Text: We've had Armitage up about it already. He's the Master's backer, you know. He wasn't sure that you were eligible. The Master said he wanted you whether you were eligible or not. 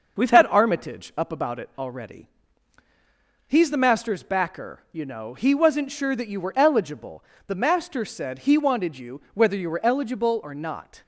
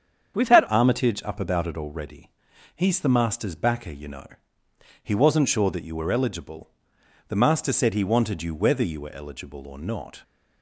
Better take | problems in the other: first | starts louder than the rest; strong; until 1.3 s; 7.5 dB // changes voice at "Armitage"; from 0.6 s on; 9.6 s long

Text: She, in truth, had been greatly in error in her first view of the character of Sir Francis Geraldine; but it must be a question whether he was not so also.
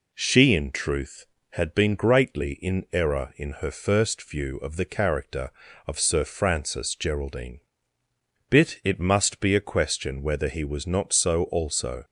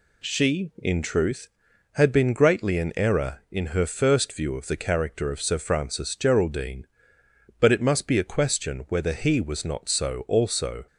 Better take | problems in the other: second | says "bit" for "but"; at 8.5 s

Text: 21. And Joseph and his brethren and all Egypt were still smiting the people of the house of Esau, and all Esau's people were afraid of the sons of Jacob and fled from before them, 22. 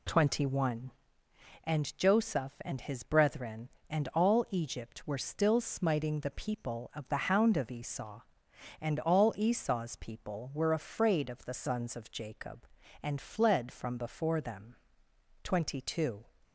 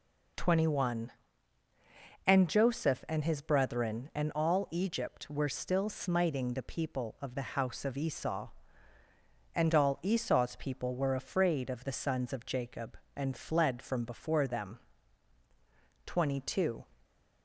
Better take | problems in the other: second | says "hound" for "house"; at 7.2 s

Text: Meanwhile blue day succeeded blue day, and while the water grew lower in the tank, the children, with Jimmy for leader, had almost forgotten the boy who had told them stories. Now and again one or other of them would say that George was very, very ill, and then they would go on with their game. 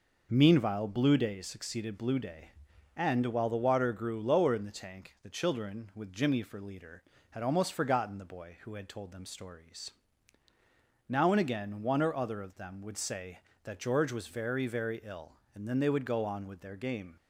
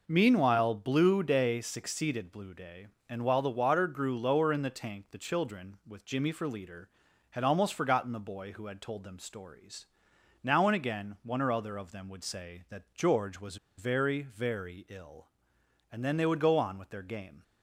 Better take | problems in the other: first | pauses between "was" and "very"; slight; at 13.5 s; 0.22 s long

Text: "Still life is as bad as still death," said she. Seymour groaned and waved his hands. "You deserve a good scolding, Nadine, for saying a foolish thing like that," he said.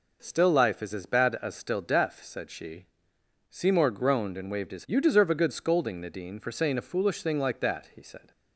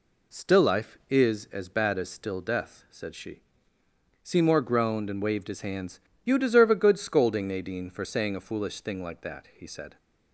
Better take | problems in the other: second | skips "hands"; at 4.8 s

